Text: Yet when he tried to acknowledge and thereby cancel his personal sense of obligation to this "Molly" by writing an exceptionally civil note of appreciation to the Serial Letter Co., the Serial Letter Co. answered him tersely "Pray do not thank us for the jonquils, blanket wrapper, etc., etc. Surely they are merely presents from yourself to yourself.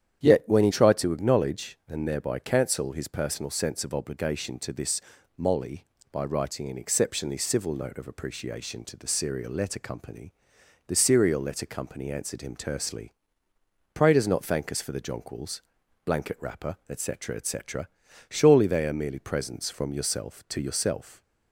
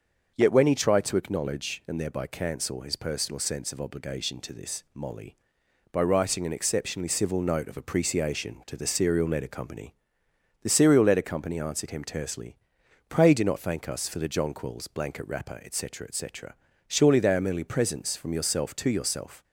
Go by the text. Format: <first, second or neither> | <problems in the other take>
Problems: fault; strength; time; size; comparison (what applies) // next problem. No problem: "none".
second | starts louder than the rest; strong; until 1.2 s; 9.5 dB; also in the second // pauses between "this" and "Molly"; at 4.9 s; 0.38 s long // pauses between "tersely" and "Pray"; noticeable; at 13.1 s; 0.80 s long; noticeable in the second // says "does" for "do"; at 14.1 s